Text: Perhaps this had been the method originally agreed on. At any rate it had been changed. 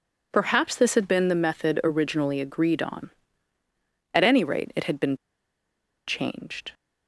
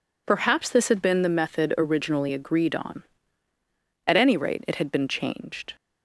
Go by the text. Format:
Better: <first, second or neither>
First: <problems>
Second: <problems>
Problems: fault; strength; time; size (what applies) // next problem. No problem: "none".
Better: second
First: pauses between "been" and "changed"; noticeable; at 5.1 s; 0.90 s long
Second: none